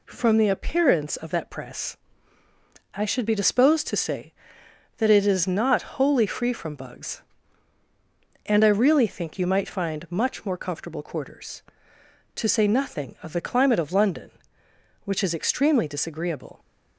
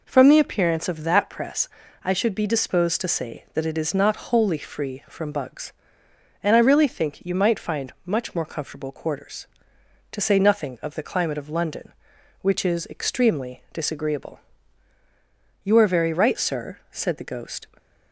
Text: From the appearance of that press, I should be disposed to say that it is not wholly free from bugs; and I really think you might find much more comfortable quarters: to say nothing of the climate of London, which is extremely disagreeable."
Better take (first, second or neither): first